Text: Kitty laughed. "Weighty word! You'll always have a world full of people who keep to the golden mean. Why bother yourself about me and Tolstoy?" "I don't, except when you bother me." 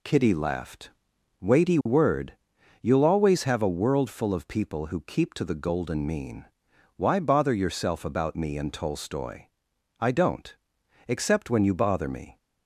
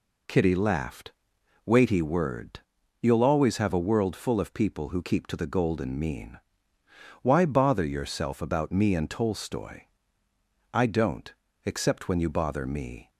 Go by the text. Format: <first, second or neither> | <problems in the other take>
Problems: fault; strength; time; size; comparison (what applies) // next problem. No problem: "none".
neither | none